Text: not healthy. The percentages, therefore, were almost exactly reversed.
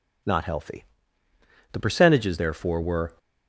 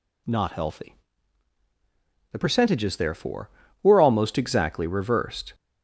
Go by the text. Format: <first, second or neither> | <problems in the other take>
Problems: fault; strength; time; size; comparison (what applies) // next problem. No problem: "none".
second | stops before "almost exactly reversed"; at 3.1 s